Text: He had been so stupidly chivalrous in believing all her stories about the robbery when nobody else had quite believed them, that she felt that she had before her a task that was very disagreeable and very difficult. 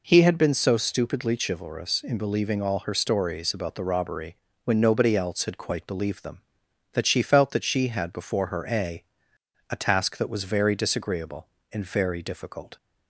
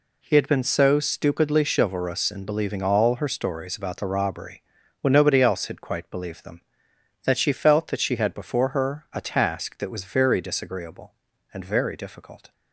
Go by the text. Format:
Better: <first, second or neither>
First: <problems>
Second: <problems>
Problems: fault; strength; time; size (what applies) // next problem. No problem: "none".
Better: second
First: pauses between "robbery" and "when"; slight; at 4.3 s; 0.28 s long // says "a" twice; at 9.7 s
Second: pauses between "robbery" and "when"; at 4.6 s; 0.38 s long